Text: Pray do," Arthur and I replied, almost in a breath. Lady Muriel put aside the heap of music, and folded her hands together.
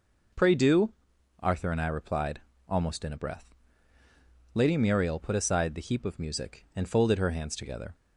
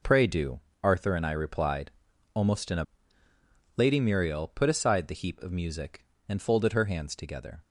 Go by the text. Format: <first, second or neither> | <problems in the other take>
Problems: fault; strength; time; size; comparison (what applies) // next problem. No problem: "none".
first | skips "breath"; at 3.2 s